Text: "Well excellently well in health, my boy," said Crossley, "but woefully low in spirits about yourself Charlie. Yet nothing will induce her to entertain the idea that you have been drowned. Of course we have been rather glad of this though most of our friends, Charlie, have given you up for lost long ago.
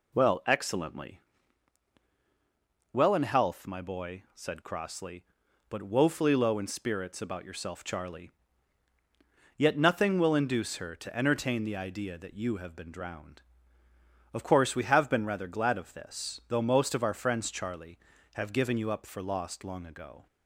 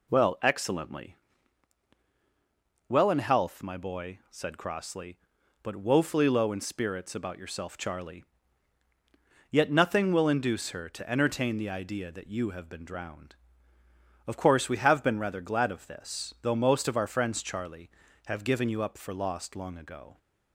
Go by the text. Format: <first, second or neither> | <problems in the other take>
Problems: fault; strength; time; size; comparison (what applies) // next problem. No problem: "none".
neither | pauses between "excellently" and "well"; strong; the same in both